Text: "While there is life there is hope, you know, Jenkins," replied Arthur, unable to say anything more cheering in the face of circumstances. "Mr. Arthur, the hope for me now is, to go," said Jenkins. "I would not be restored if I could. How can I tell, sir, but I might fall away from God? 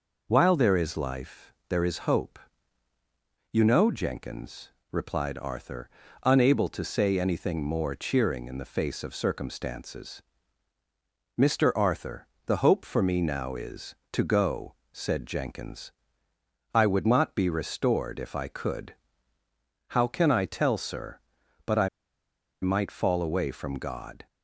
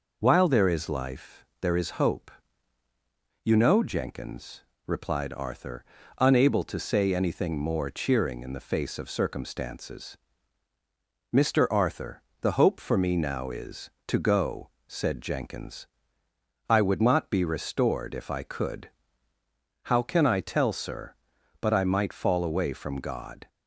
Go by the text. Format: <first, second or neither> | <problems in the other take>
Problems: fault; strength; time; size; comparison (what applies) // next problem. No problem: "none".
second | pauses between "life" and "there"; slight; at 1.5 s; 0.16 s long; slight in the second // pauses between "I" and "might"; noticeable; at 21.8 s; 0.74 s long